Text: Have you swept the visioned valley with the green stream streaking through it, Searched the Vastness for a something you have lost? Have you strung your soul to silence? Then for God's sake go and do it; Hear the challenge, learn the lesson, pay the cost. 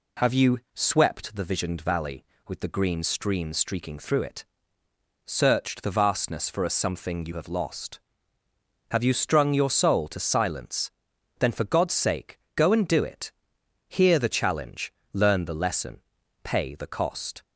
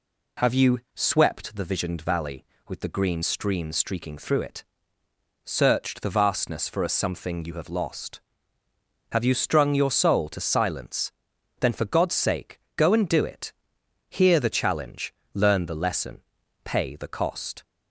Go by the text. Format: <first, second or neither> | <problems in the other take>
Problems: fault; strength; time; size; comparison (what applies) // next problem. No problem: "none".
neither | pauses between "you" and "swept"; slight; the same in both // pauses between "sake" and "go"; slight; the same in both